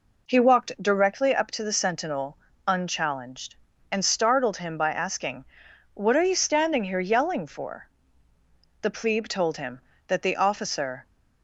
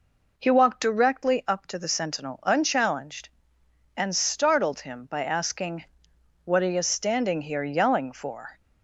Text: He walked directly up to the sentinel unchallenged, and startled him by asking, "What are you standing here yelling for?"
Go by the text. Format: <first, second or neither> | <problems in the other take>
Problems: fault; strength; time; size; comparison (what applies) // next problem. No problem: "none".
second | pauses between "sentinel" and "unchallenged"; slight; at 2.3 s; 0.30 s long // goes on to say "The plebe told him that the officer"; strong; from 8.8 s on; 2.2 s long